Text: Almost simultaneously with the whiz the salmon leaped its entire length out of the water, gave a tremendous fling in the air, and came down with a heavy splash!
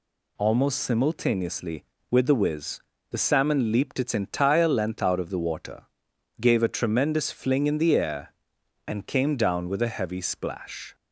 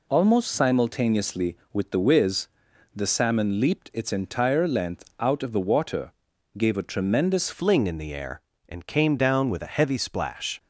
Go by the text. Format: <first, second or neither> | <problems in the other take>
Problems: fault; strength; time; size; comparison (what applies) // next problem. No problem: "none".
first | pauses between "whiz" and "the"; noticeable; at 2.4 s; 0.48 s long; slight in the first // changes voice at "fling"; from 7.5 s on; 3.0 s long